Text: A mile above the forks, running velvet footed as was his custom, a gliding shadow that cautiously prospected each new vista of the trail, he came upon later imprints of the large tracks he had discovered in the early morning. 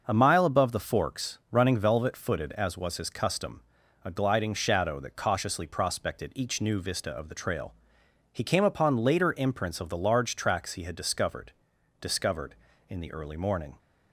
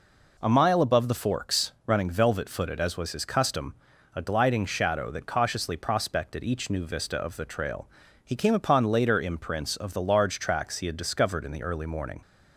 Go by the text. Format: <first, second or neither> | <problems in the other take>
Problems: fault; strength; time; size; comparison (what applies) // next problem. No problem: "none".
second | says "discovered" twice; at 12.0 s